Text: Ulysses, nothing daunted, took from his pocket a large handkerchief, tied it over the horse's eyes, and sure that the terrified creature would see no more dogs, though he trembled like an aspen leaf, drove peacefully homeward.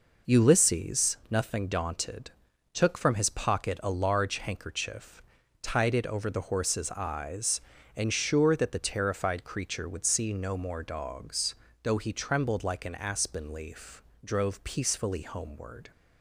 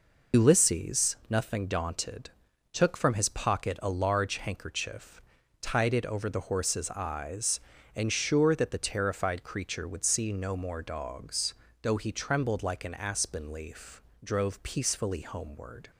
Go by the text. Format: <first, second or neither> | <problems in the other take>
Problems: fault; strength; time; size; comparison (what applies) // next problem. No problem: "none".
first | loses the start of "Ulysses"; at 0.3 s; 80 ms